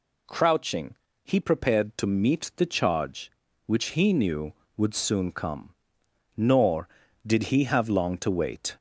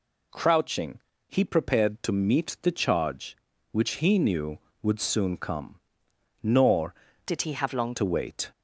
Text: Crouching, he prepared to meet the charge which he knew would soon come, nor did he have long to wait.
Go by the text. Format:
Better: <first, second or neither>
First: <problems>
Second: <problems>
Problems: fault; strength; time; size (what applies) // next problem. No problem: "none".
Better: first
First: none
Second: changes voice from "did" to "long"; from 7.2 to 7.9 s; 0.7 s long